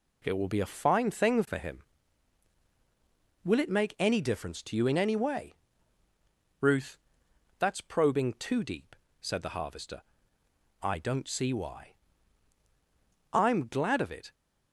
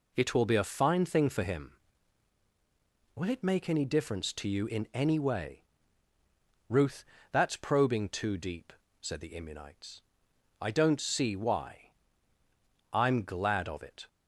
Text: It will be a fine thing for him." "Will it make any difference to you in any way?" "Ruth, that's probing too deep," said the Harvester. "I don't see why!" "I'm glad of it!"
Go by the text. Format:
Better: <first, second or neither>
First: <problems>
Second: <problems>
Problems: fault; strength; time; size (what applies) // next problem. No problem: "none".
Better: first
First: none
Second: says "Immunites" for "Harvester"; at 9.3 s